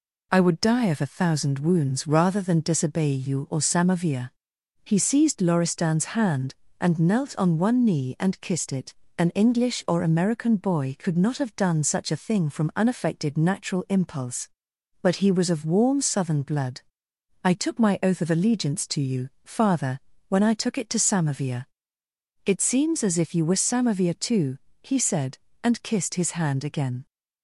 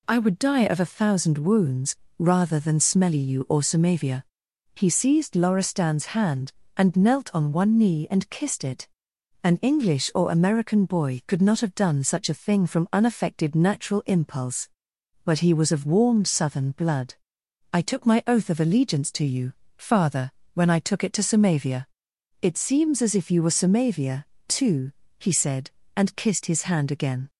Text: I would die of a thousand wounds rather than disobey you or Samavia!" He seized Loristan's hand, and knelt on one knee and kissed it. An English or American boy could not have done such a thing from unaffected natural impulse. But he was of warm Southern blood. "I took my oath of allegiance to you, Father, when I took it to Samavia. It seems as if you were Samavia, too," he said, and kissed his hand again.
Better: first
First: none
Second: pauses between "wounds" and "rather"; slight; at 1.9 s; 0.24 s long // says "smelly" for "disobey"; at 2.8 s

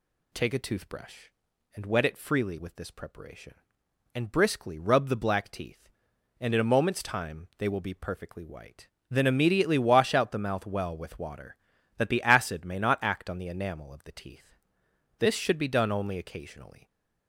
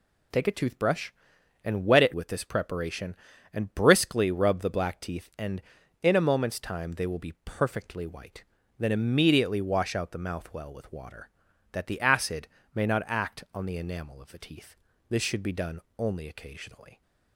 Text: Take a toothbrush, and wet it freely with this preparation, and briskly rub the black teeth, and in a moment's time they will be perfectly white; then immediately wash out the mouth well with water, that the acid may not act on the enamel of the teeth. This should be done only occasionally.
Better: first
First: none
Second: skips "freely"; at 2.1 s // pauses between "acid" and "may"; slight; at 12.4 s; 0.26 s long // pauses between "done" and "only"; slight; at 15.8 s; 0.18 s long

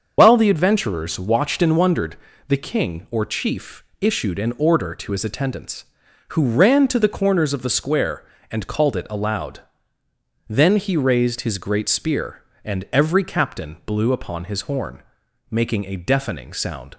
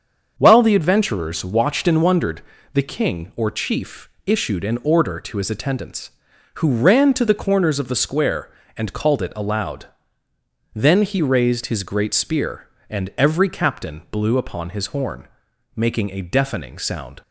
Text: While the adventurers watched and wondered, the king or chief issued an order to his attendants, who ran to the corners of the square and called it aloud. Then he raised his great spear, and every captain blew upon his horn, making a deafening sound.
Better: second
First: loses the start of "While"; at 0.1 s; 55 ms // starts louder than the rest; until 1.2 s; 6.5 dB // pauses between "chief" and "issued"; slight; at 3.8 s; 0.18 s long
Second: starts louder than the rest; until 1.3 s; 7 dB // pauses between "chief" and "issued"; slight; at 4.0 s; 0.18 s long

